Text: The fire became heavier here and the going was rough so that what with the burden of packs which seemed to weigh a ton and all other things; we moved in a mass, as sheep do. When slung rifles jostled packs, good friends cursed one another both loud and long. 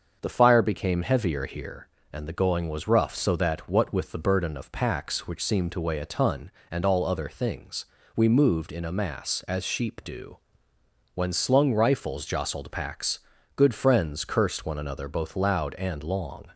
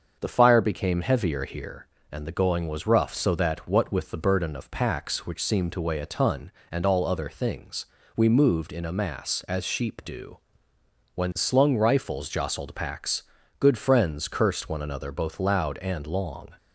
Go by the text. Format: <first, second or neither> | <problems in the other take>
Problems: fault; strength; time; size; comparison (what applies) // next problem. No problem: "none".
neither | starts louder than the rest; the same in both